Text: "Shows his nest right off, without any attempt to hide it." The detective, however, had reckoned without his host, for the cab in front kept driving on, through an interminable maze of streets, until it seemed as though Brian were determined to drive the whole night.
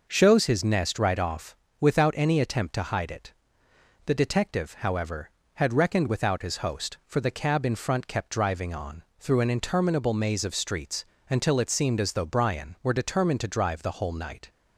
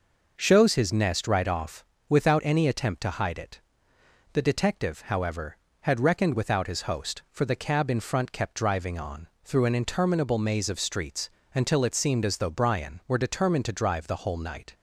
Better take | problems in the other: neither | none

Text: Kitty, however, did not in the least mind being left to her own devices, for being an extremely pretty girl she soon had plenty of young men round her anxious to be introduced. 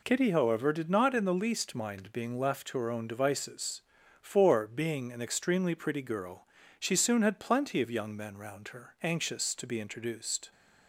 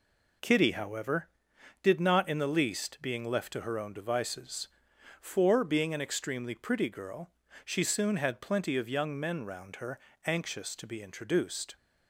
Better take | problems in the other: first | skips "mind"; at 2.9 s // pauses between "girl" and "she"; slight; at 7.3 s; 0.34 s long; slight in the first // pauses between "her" and "anxious"; slight; at 9.9 s; 0.26 s long

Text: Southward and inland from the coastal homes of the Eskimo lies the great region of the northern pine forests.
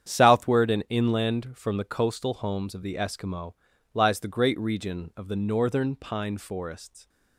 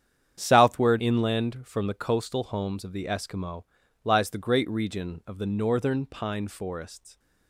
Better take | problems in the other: first | starts louder than the rest; strong; until 1.3 s; 8.5 dB; strong in the first // skips "and"; at 0.9 s // pauses between "Eskimo" and "lies"; at 3.6 s; 0.38 s long; also in the first

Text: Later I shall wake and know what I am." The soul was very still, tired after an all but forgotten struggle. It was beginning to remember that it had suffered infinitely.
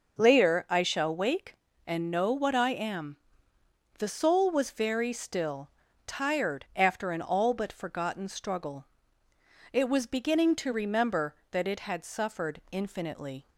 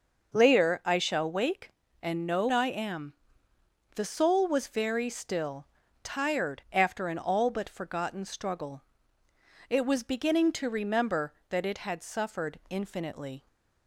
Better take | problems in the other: first | skips "what"; at 2.4 s

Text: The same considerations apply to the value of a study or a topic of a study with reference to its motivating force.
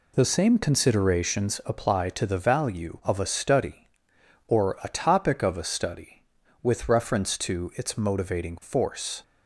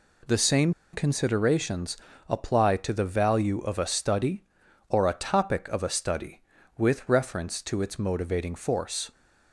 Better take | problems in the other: first | pauses between "same" and "considerations"; slight; at 0.7 s; 0.20 s long // pauses between "considerations" and "apply"; slight; at 1.9 s; 0.32 s long

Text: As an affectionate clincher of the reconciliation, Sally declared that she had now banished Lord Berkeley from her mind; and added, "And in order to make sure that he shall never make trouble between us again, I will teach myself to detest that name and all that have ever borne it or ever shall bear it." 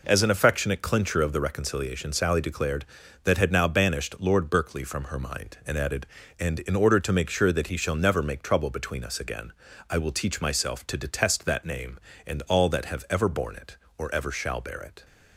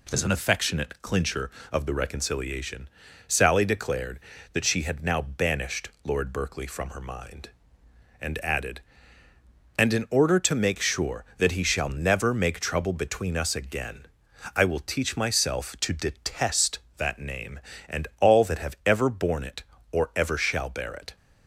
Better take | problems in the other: second | skips "she"; at 3.3 s

